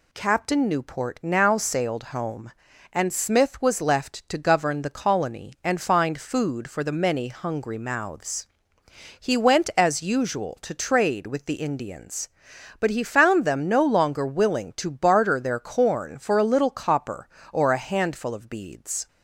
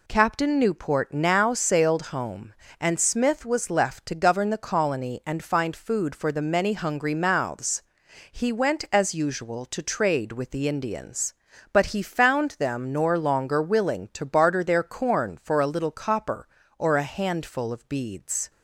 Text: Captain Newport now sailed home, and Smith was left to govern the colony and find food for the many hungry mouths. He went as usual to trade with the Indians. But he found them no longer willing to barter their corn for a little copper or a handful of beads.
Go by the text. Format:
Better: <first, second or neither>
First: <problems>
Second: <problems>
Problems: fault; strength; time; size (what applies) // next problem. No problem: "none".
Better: first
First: none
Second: says "nor" for "no"; at 12.9 s